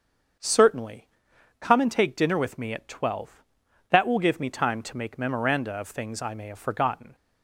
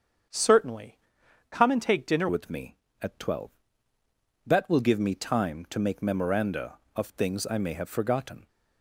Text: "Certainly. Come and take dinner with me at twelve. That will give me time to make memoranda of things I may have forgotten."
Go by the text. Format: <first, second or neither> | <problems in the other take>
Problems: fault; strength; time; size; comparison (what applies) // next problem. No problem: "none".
first | starts louder than the rest; strong; until 1.8 s; 7.5 dB; also in the first // changes voice at "with"; from 2.2 s on; 6.2 s long